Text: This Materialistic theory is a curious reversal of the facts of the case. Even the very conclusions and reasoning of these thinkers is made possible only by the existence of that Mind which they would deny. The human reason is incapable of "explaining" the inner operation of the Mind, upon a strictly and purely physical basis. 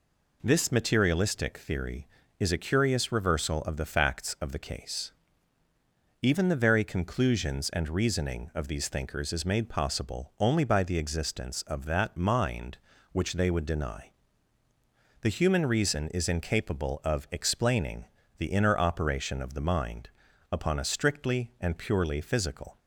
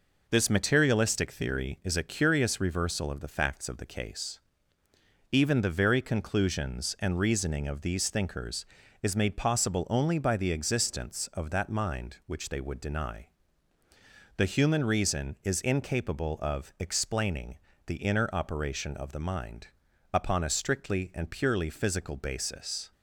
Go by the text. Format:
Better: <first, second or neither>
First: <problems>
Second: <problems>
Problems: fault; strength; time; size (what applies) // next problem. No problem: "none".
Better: second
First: pauses between "explaining" and "the"; slight; at 18.0 s; 0.32 s long // stops before "basis"; at 22.7 s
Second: pauses between "explaining" and "the"; slight; at 17.5 s; 0.28 s long